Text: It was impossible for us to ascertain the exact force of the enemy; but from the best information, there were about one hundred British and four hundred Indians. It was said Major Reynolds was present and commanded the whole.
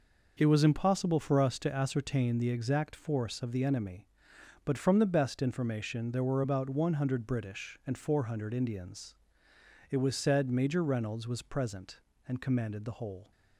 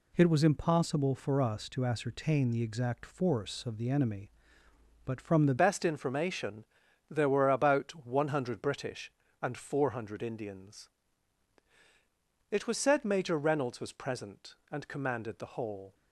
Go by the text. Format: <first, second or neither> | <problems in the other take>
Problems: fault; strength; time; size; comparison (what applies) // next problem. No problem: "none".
first | changes voice at "best"; from 5.5 s on; 10.4 s long